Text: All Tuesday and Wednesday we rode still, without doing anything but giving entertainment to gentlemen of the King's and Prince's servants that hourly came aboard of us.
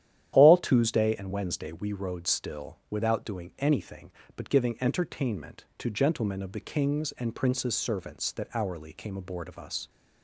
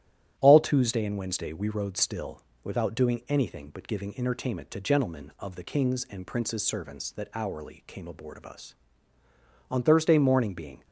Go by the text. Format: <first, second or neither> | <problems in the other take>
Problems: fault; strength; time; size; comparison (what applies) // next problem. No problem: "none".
first | starts louder than the rest; strong; until 1.3 s; 12 dB; strong in the first // goes on to say "On Thursday morning being"; noticeable; from 9.7 s on; 1.1 s long